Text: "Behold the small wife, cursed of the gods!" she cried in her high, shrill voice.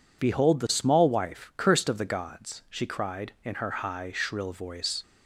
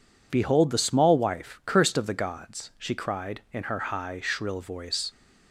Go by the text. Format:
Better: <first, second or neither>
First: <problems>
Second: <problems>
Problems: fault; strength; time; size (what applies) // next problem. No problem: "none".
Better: neither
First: none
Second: none